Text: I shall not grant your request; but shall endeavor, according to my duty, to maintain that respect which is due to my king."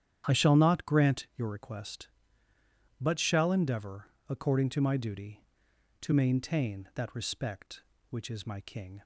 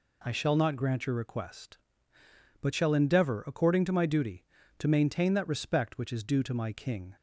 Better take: second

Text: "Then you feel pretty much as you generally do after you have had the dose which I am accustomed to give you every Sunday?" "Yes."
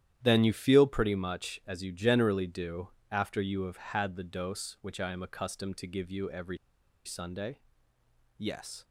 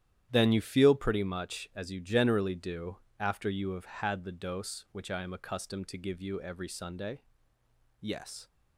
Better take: second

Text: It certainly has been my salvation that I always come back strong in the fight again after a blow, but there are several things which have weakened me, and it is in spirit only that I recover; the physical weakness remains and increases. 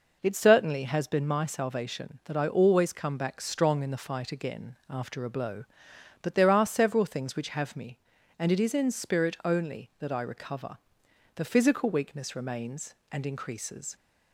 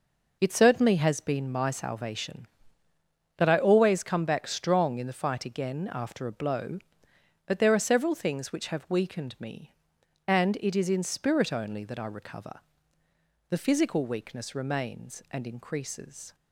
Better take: second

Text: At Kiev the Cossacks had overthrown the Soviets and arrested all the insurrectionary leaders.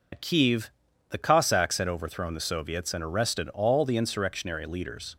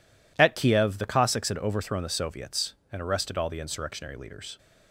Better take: second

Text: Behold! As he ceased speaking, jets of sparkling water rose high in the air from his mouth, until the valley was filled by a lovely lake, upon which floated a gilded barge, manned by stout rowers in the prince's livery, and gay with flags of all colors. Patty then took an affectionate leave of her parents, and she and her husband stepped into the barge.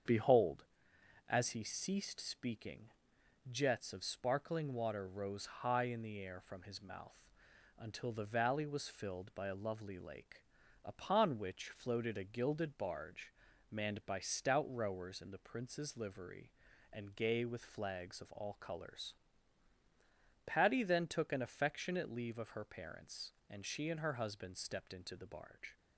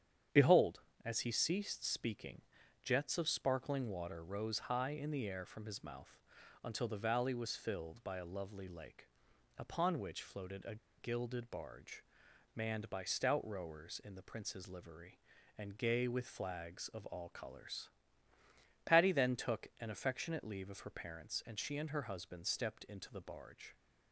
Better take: first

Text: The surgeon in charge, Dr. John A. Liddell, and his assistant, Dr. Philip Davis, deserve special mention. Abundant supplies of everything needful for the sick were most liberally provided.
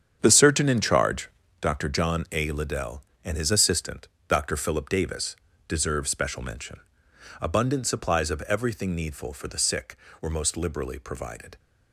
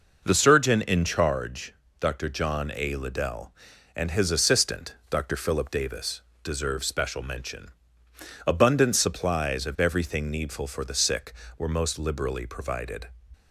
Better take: second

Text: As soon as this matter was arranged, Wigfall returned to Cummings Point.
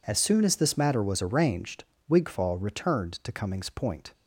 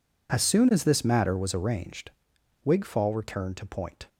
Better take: first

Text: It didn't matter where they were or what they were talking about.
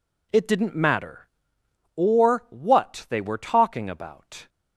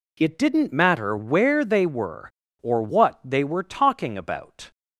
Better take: second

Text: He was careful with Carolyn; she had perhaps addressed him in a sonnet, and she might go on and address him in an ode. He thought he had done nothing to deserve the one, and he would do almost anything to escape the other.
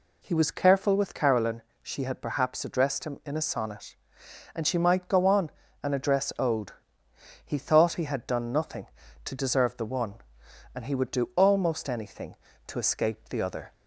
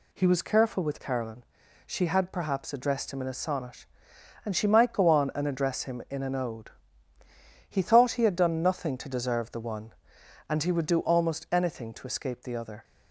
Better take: second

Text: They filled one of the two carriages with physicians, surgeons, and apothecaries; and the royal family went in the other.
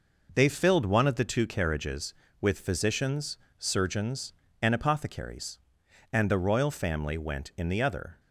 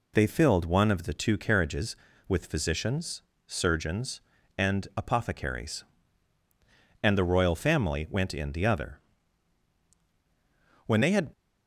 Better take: first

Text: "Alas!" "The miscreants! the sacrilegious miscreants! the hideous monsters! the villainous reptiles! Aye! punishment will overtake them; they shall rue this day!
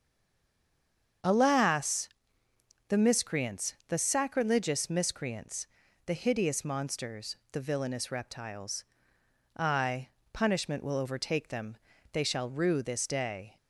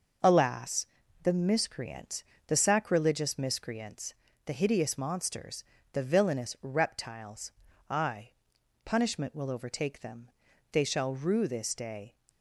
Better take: second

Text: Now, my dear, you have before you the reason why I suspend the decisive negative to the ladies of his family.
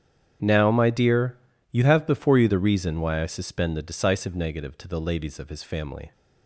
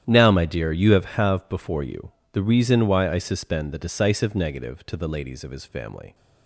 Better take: first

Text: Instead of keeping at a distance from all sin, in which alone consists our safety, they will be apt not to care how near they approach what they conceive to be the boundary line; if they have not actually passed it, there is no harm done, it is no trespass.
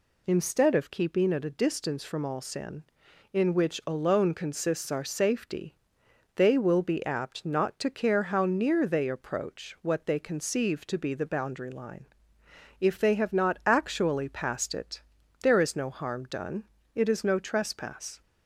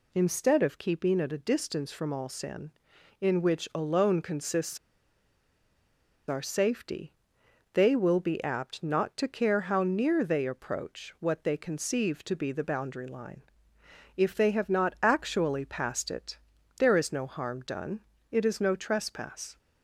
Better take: first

